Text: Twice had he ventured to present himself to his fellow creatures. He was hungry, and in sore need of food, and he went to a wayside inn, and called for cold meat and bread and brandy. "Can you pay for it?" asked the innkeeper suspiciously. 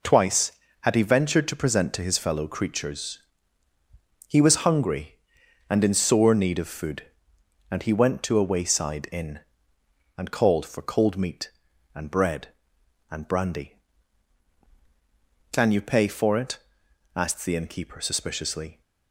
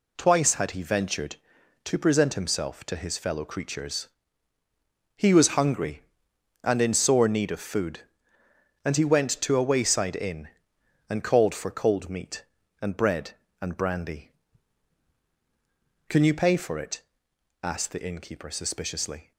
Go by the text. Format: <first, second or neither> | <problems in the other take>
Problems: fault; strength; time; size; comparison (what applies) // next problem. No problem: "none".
second | skips "himself"; at 1.9 s